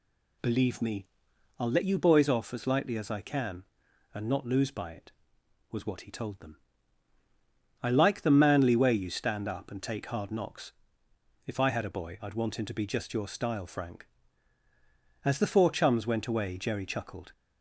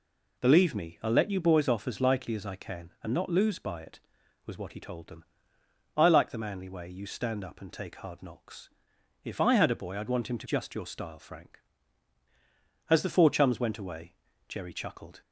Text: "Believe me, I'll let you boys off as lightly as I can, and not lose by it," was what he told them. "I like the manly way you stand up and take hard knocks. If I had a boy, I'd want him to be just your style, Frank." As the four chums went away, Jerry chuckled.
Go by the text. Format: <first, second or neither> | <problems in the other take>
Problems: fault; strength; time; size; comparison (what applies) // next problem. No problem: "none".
first | skips "be"; at 10.4 s